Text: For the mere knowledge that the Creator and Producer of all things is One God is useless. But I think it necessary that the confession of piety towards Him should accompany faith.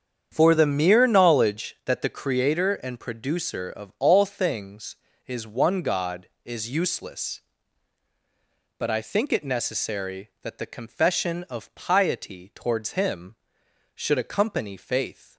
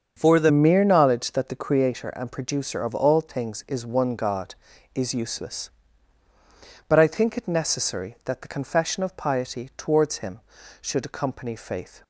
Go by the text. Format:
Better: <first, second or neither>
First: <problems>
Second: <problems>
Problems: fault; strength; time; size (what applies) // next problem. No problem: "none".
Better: first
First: starts louder than the rest; strong; until 1.3 s; 8 dB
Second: starts louder than the rest; strong; until 1.1 s; 7.5 dB // changes voice at "mere"; from 0.5 s on; 11.5 s long